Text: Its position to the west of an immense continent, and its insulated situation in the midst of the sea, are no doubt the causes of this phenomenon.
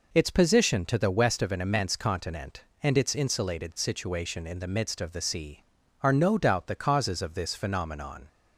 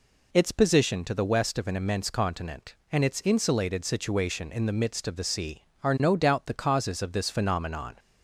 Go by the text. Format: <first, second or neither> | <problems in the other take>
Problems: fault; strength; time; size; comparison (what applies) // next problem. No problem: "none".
neither | none